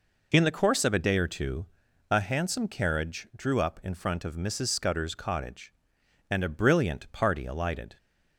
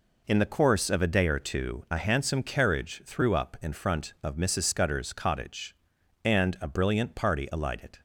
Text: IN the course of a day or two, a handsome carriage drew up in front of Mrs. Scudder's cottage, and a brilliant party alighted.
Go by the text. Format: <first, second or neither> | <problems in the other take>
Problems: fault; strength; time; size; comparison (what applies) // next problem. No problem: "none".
first | says "threw" for "drew"; at 3.0 s